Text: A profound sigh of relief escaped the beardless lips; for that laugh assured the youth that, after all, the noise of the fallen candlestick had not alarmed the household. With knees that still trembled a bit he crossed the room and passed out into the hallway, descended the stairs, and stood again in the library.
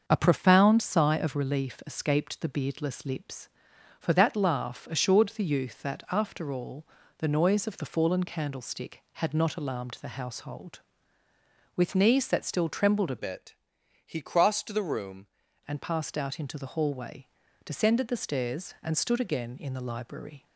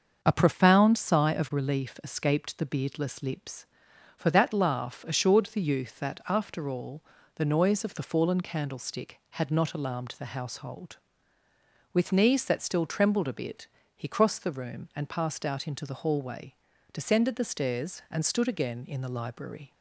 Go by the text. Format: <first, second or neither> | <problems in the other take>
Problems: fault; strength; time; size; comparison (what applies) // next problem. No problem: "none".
second | starts louder than the rest; until 1.0 s; 6.5 dB; also in the second // changes voice from "bit" to "room"; from 13.1 to 15.2 s; 2.1 s long // pauses between "bit" and "he"; noticeable; at 13.5 s; 0.52 s long; slight in the second